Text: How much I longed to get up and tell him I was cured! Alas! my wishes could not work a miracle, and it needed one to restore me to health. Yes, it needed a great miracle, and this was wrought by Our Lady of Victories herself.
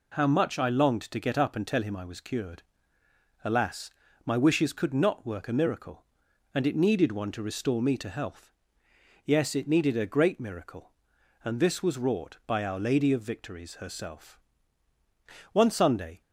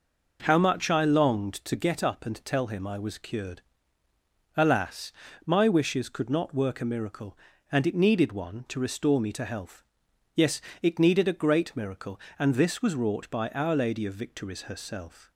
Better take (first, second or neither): second